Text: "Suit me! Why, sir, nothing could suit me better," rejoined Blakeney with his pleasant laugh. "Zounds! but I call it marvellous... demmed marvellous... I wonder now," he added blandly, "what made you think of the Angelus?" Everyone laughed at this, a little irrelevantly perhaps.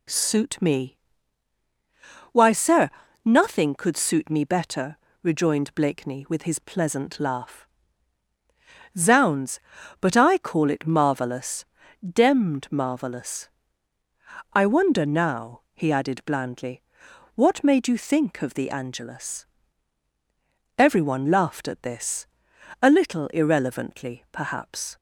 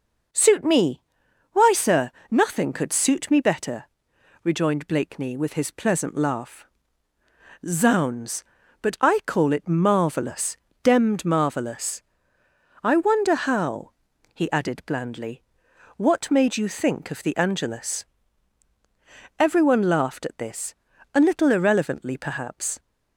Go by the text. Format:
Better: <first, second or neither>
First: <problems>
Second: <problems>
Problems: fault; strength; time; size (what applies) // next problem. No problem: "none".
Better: first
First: none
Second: says "how" for "now"; at 13.3 s